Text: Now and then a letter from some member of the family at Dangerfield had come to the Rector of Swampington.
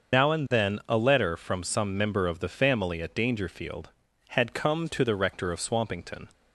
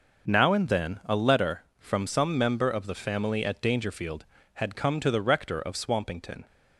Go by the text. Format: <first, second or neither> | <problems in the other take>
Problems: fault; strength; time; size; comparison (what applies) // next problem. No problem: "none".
second | loses the start of "Now"; at 0.1 s; 85 ms // starts louder than the rest; until 1.2 s; 6.5 dB; also in the second